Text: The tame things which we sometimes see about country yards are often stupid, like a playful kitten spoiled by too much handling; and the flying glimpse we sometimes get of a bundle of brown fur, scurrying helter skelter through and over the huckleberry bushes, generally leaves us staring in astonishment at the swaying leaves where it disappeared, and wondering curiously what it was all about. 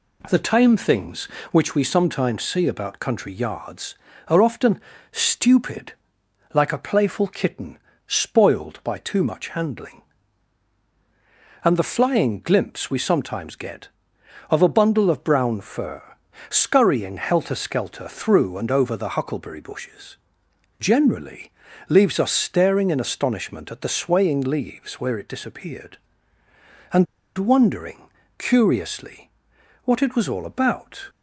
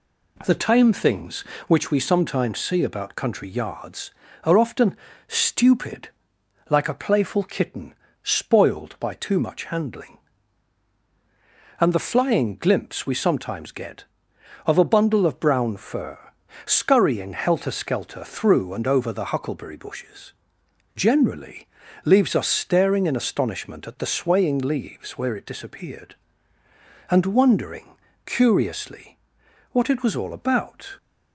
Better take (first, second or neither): second